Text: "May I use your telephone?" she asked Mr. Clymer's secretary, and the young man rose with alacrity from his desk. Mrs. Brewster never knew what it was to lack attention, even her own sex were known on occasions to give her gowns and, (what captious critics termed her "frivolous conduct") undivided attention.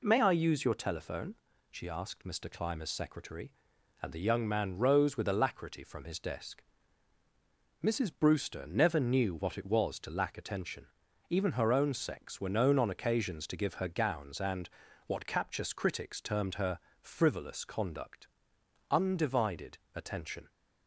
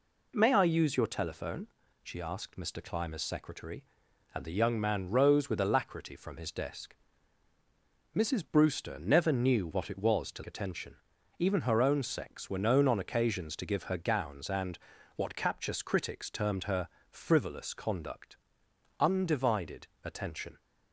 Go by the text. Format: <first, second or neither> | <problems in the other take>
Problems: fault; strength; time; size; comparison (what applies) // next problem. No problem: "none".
first | skips "lack"; at 10.4 s // pauses between "her" and "frivolous"; slight; at 16.8 s; 0.20 s long; slight in the first // pauses between "undivided" and "attention"; slight; at 19.8 s; 0.16 s long; slight in the first